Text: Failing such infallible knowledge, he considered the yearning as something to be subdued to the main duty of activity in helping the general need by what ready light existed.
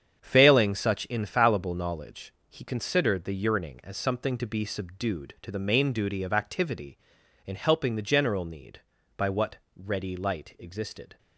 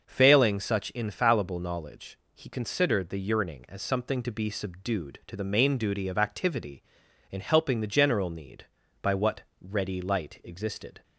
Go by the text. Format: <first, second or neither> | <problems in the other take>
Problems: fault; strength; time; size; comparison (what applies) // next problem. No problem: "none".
second | gets quieter; strong; throughout; 8.5 dB // starts louder than the rest; strong; until 1.2 s; 8 dB; noticeable in the second // pauses between "what" and "ready"; slight; at 9.5 s; 0.20 s long; slight in the second